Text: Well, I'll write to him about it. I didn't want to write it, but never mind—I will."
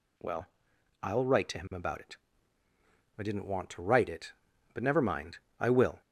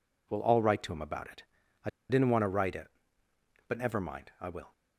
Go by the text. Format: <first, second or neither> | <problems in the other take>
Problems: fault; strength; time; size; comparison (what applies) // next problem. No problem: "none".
first | pauses between "I" and "didn't"; slight; at 1.8 s; 0.20 s long